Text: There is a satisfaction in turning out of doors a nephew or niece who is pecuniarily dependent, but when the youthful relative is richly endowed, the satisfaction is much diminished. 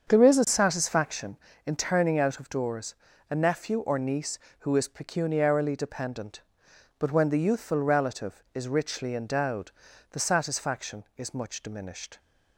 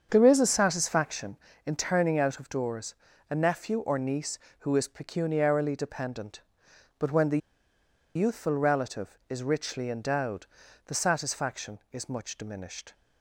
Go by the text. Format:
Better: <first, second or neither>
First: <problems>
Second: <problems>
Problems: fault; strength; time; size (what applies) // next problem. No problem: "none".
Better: first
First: starts louder than the rest; strong; until 1.1 s; 7 dB // pauses between "doors" and "a"; slight; at 2.9 s; 0.34 s long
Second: starts louder than the rest; strong; until 1.1 s; 7 dB // pauses between "doors" and "a"; slight; at 2.9 s; 0.34 s long // pauses between "the" and "youthful"; noticeable; at 7.3 s; 0.77 s long